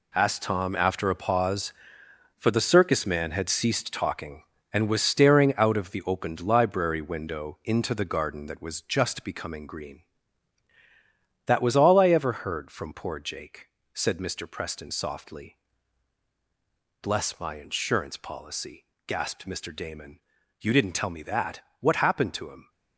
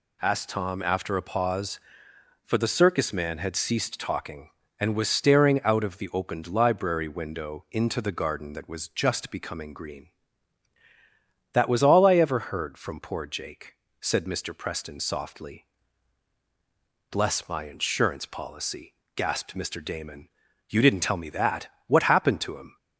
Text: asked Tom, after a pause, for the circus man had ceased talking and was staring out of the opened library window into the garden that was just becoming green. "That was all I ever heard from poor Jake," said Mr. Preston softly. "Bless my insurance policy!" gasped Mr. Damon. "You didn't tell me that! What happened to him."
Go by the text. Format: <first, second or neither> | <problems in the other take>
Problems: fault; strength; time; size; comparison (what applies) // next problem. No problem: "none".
second | gets quieter; strong; throughout; 10 dB